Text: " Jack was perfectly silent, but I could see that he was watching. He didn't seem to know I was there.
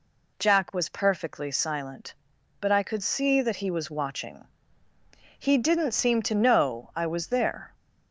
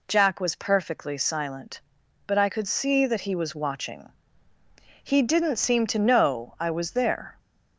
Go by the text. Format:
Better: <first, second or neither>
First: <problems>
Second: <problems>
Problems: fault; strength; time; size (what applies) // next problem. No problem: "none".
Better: neither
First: none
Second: none